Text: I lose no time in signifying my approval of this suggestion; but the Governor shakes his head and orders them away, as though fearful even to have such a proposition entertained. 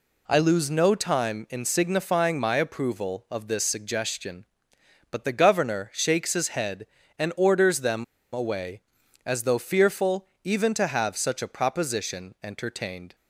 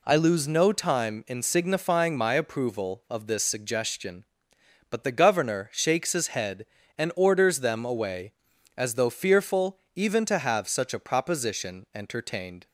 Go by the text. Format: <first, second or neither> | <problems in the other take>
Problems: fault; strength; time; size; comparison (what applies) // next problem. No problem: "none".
second | pauses between "them" and "away"; slight; at 8.0 s; 0.30 s long // pauses between "fearful" and "even"; slight; at 10.2 s; 0.16 s long; slight in the second